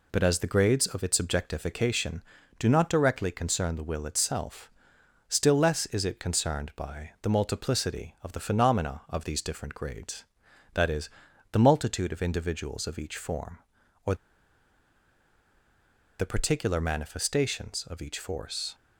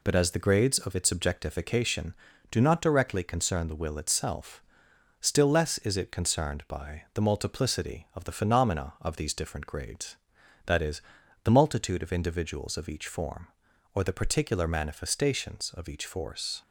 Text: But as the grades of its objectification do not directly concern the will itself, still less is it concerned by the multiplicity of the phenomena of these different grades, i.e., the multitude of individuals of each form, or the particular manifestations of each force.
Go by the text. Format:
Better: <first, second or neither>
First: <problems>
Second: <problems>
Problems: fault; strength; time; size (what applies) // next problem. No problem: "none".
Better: second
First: pauses between "or" and "the"; strong; at 14.1 s; 2.0 s long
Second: none